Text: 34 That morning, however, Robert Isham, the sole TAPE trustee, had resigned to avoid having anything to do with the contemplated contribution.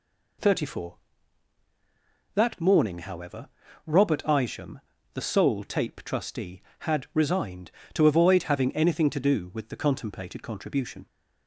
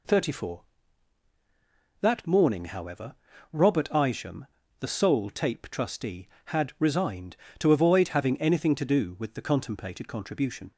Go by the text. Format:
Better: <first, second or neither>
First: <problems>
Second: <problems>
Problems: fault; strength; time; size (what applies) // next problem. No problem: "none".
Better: neither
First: none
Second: none